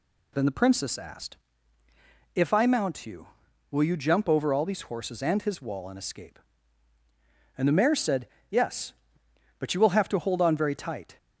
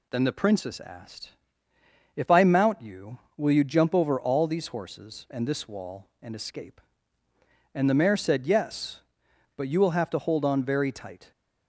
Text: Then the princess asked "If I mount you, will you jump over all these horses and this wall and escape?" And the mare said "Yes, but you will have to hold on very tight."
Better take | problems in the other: second | pauses between "asked" and "If"; noticeable; at 1.3 s; 0.98 s long; noticeable in the second // says "his" for "this"; at 5.4 s // pauses between "said" and "Yes"; slight; at 8.2 s; 0.22 s long

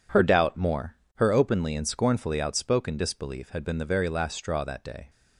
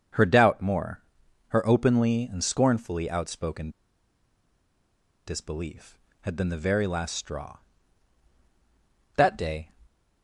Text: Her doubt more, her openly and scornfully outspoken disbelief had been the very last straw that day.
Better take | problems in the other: first | starts louder than the rest; until 1.6 s; 7 dB // pauses between "outspoken" and "disbelief"; strong; at 3.7 s; 1.5 s long

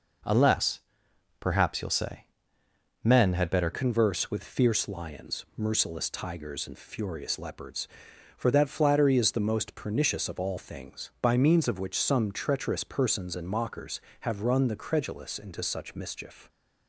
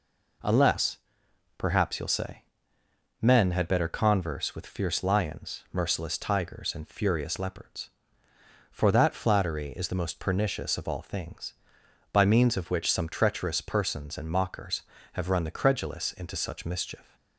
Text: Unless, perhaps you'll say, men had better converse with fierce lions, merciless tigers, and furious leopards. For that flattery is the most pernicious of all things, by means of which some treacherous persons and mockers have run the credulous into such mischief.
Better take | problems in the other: second | changes voice at "converse"; from 3.7 s on; 12.7 s long

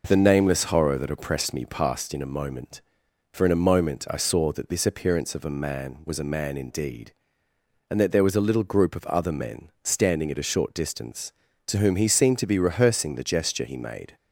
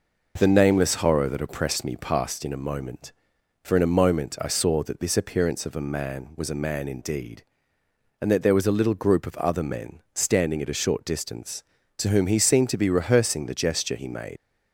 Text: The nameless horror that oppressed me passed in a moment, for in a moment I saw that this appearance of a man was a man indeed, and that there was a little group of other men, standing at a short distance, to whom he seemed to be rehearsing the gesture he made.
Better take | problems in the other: first | leaves "made" unfinished; at 14.3 s; 100 ms

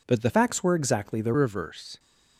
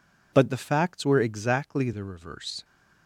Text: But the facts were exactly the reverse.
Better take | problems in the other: second | changes voice from "facts" to "the"; from 0.2 to 1.3 s; 1.1 s long

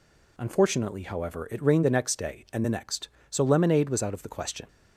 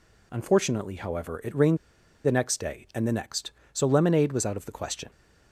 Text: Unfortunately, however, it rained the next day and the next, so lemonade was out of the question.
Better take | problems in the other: first | pauses between "rained" and "the"; noticeable; at 1.7 s; 0.48 s long

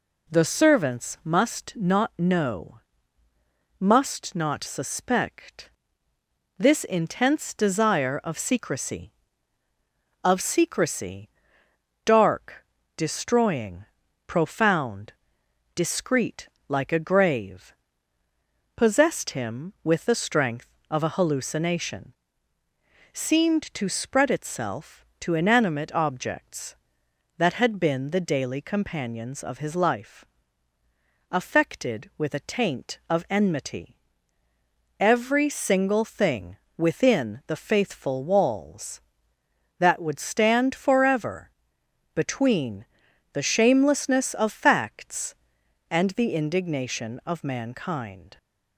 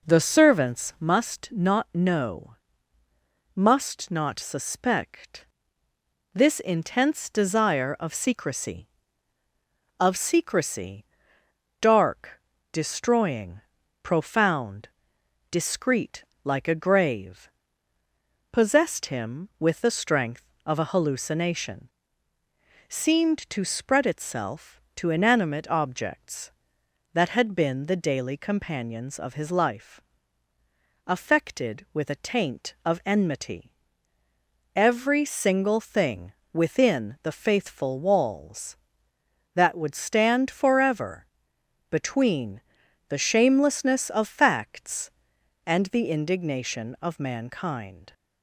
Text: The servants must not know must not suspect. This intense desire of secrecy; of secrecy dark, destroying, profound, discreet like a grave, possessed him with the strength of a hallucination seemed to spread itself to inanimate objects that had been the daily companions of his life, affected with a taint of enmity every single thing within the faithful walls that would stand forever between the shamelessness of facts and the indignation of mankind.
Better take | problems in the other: first | starts louder than the rest; noticeable; until 1.1 s; 4.5 dB // pauses between "know" and "must"; at 2.5 s; 1.0 s long; also in the first // pauses between "secrecy" and "dark"; noticeable; at 11.0 s; 0.74 s long; noticeable in the first // pauses between "discreet" and "like"; slight; at 16.2 s; 0.18 s long; slight in the first // pauses between "hallucination" and "seemed"; at 21.8 s; 1.0 s long; also in the first // pauses between "enmity" and "every"; at 33.7 s; 1.0 s long; also in the first // pauses between "thing" and "within"; slight; at 36.3 s; 0.20 s long; slight in the first // pauses between "forever" and "between"; noticeable; at 41.2 s; 0.64 s long; noticeable in the first // pauses between "between" and "the"; noticeable; at 42.6 s; 0.48 s long; noticeable in the first

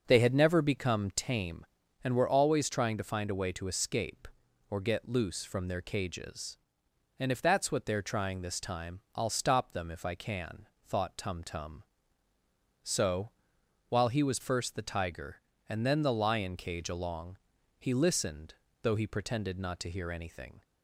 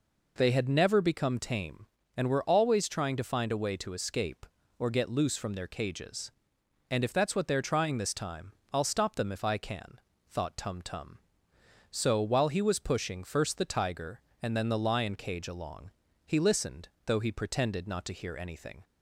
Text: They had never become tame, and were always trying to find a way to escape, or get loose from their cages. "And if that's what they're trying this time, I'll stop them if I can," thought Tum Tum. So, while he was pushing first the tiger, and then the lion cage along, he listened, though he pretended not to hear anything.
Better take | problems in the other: second | starts louder than the rest; noticeable; until 1.0 s; 6 dB // skips "pushing"; at 14.3 s

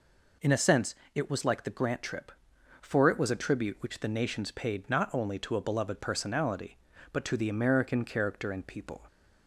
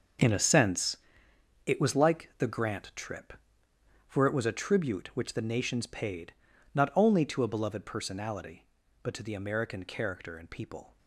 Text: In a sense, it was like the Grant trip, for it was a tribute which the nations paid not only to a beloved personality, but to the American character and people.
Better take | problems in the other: first | gets quieter; strong; throughout; 12.5 dB // pauses between "paid" and "not"; at 6.3 s; 0.40 s long

